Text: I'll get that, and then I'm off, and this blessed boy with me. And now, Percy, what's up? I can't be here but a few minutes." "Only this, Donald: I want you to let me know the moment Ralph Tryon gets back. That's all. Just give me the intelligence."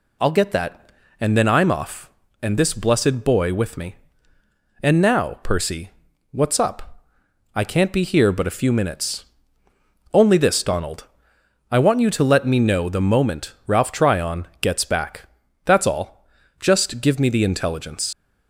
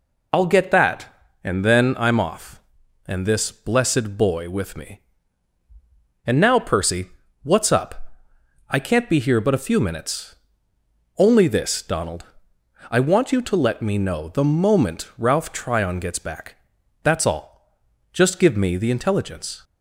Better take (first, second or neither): second